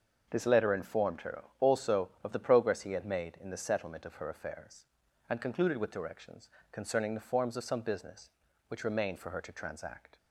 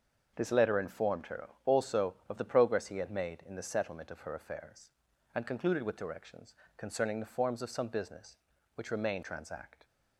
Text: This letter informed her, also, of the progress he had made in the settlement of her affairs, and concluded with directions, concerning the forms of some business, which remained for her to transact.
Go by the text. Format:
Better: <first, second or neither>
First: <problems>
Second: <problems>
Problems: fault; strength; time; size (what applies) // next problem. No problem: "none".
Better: first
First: starts louder than the rest; until 1.3 s; 6.5 dB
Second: starts louder than the rest; until 1.3 s; 6.5 dB // skips "for her to"; at 9.2 s